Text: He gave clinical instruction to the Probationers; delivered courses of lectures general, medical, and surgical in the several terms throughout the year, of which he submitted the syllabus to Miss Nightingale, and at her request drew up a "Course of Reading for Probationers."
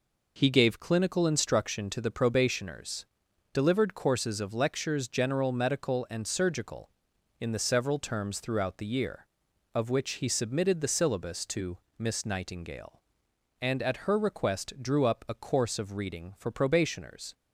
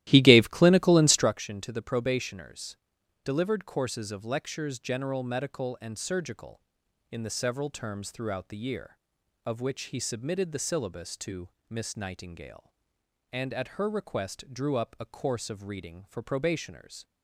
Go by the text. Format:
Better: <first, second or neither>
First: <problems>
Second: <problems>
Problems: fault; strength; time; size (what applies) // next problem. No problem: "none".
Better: first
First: pauses between "to" and "Miss"; slight; at 11.7 s; 0.18 s long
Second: starts louder than the rest; strong; until 1.3 s; 14.5 dB // pauses between "to" and "Miss"; slight; at 11.4 s; 0.18 s long